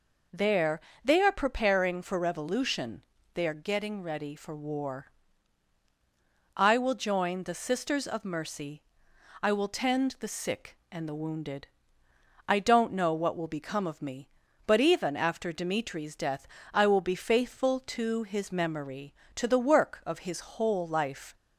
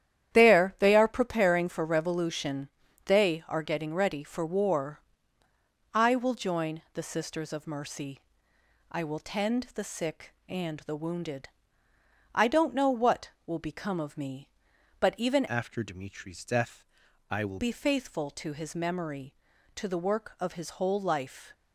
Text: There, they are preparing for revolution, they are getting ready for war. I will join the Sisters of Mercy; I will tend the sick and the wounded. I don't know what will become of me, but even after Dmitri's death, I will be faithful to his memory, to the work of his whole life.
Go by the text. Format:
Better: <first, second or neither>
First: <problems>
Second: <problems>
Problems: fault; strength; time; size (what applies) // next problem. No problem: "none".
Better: first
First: none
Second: starts louder than the rest; strong; until 1.3 s; 10.5 dB // changes voice from "after" to "will"; from 15.4 to 17.5 s; 2.1 s long